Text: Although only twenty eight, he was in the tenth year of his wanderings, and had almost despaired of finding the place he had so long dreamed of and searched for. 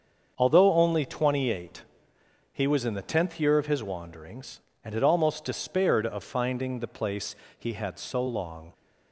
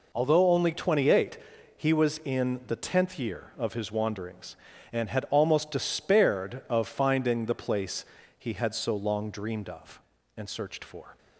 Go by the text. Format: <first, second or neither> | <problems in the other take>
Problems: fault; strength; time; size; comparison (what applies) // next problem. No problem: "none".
second | starts louder than the rest; until 1.3 s; 7 dB // pauses between "place" and "he"; slight; at 7.3 s; 0.24 s long; slight in the second // stops before "dreamed of and searched for"; at 8.7 s